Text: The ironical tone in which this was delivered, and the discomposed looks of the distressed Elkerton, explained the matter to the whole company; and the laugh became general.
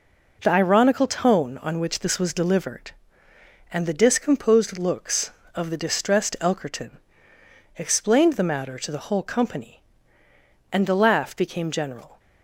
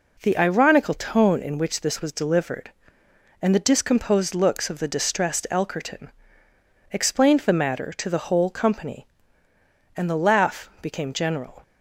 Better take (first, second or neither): second